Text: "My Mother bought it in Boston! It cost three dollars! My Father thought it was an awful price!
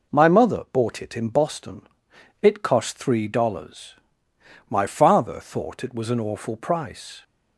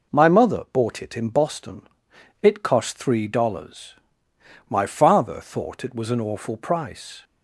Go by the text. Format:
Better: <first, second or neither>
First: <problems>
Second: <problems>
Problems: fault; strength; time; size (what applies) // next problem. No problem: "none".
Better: neither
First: none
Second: none